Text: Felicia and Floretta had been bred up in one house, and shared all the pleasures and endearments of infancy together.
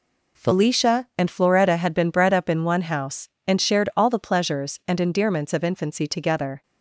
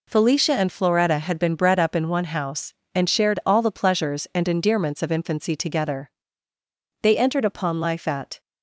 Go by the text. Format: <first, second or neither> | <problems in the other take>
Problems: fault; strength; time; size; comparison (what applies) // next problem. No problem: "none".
first | goes on to say "They entered upon life at"; from 7.0 s on; 1.3 s long